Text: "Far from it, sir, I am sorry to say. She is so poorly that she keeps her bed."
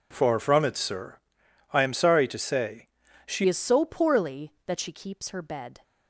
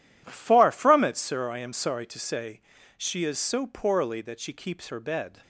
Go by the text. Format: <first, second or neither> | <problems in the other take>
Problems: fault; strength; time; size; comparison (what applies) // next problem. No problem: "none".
second | changes voice at "is"; from 3.4 s on; 2.4 s long